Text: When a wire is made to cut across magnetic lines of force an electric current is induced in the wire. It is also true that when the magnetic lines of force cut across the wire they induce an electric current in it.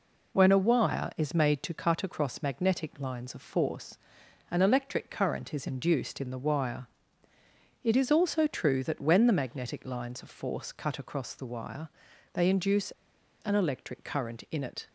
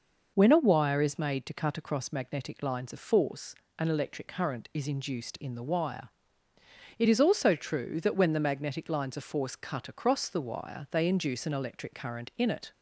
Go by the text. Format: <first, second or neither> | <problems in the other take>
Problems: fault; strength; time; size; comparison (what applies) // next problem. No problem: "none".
second | pauses between "force" and "an"; noticeable; at 3.9 s; 0.52 s long; slight in the second // pauses between "wire" and "they"; at 11.8 s; 0.44 s long // pauses between "induce" and "an"; noticeable; at 12.9 s; 0.50 s long